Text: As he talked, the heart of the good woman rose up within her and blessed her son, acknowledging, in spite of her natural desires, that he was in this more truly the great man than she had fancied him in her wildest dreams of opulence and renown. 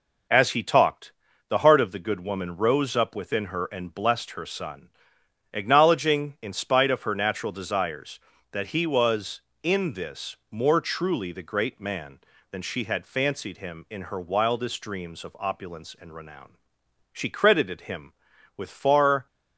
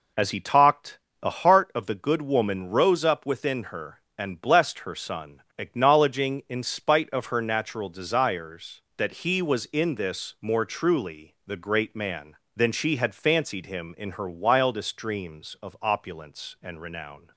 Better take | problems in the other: second | goes on to say "She credited him with far"; strong; from 17.1 s on; 2.1 s long

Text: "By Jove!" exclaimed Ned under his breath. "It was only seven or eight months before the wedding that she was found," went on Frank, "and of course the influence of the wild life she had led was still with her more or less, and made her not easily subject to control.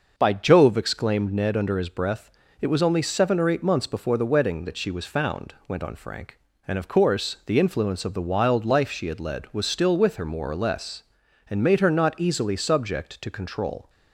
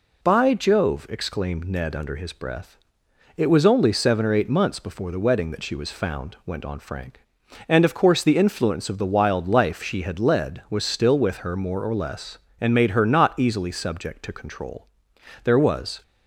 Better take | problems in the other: first | goes on to say "There was"; from 15.4 s on; 0.58 s long

